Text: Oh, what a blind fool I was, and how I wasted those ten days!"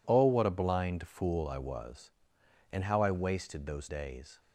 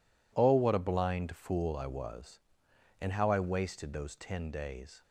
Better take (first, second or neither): second